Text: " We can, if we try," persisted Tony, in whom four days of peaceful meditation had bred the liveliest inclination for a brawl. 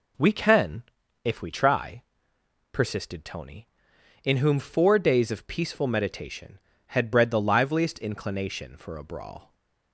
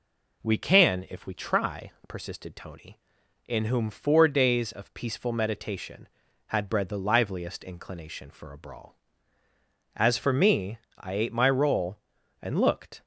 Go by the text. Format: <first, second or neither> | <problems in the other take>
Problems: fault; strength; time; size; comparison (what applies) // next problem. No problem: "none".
first | goes on to say "As for me I ate my roll and looked"; strong; from 9.9 s on; 3.0 s long